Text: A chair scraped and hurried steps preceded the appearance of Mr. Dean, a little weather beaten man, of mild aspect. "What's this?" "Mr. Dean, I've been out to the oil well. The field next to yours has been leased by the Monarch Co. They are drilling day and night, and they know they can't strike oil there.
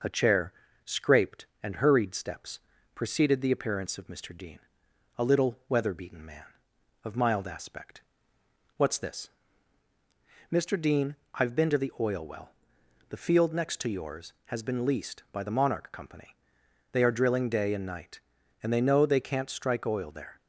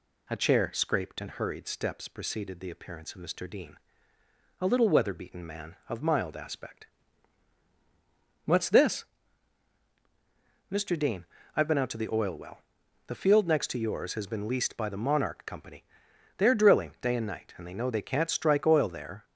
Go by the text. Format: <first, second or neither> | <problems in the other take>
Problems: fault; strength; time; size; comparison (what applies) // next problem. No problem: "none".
second | pauses between "chair" and "scraped"; slight; at 0.5 s; 0.32 s long // pauses between "steps" and "preceded"; slight; at 2.5 s; 0.36 s long // skips "out"; at 11.7 s